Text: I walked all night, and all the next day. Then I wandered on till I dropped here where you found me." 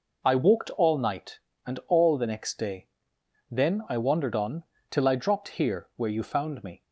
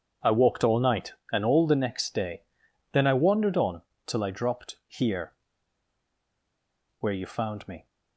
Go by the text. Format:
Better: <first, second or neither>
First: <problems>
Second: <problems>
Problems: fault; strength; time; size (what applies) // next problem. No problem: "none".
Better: first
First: pauses between "on" and "till"; slight; at 4.6 s; 0.24 s long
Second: pauses between "on" and "till"; slight; at 3.8 s; 0.24 s long // pauses between "here" and "where"; strong; at 5.3 s; 1.6 s long